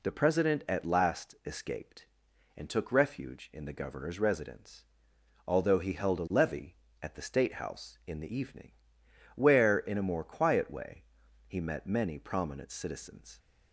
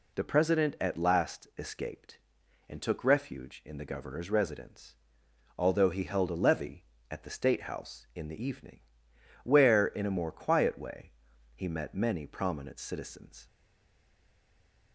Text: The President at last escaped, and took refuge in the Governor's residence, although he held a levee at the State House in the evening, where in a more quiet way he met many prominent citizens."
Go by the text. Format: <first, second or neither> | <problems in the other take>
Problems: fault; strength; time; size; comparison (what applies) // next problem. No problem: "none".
first | pauses between "way" and "he"; at 11.1 s; 0.42 s long; also in the first // stays silent after the last word; noticeable; from 13.4 s on; 1.5 s long